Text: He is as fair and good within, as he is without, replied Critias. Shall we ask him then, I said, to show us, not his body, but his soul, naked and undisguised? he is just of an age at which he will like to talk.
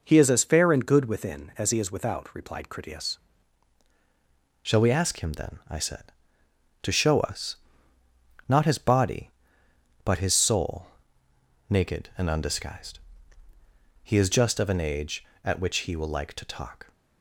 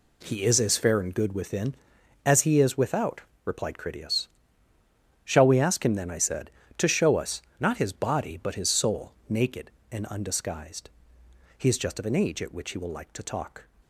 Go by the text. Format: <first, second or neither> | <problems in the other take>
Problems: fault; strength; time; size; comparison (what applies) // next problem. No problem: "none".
second | changes voice at "Shall"; from 4.6 s on; 12.3 s long